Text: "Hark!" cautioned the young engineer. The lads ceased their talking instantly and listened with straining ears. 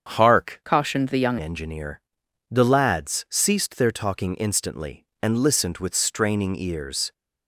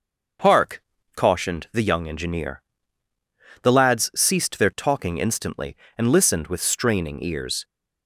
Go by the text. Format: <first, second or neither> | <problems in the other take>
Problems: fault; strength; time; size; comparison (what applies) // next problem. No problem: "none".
second | starts louder than the rest; strong; until 1.1 s; 7.5 dB; also in the second // changes voice from "cautioned" to "young"; from 0.6 to 1.3 s; 0.7 s long